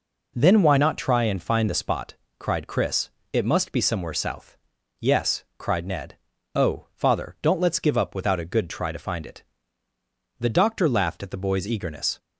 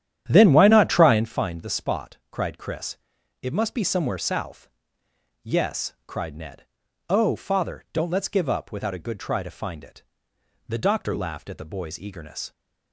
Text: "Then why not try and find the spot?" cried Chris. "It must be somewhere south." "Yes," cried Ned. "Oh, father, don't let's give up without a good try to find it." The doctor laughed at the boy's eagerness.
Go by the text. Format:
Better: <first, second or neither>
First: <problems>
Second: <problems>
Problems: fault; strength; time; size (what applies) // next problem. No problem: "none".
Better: first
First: none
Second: starts louder than the rest; strong; until 1.4 s; 10 dB